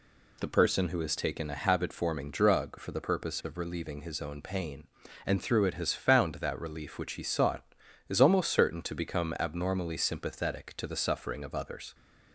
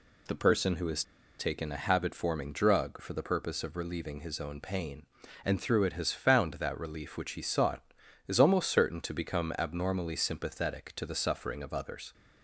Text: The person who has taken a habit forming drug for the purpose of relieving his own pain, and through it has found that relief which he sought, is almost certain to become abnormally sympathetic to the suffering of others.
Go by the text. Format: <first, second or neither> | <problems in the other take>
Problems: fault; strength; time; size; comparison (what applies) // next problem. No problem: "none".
first | pauses between "has" and "taken"; at 1.0 s; 0.36 s long